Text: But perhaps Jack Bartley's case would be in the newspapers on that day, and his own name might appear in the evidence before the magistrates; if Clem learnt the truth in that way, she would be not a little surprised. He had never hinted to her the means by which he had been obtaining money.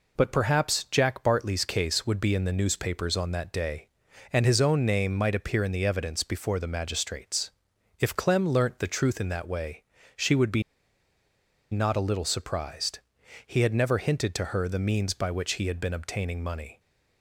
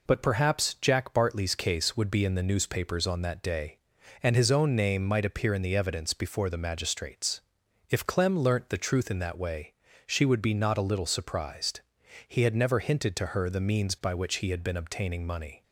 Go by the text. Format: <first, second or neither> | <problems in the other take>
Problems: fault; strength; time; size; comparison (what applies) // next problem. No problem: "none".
second | pauses between "be" and "not"; at 10.6 s; 1.0 s long